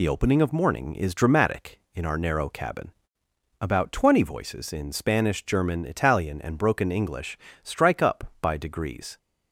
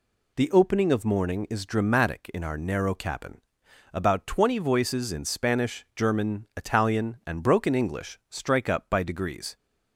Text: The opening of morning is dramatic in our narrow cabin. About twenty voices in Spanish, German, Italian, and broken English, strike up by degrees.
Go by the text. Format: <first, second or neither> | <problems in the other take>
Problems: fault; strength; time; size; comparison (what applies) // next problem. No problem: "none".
second | loses the start of "The"; at 0.0 s; 30 ms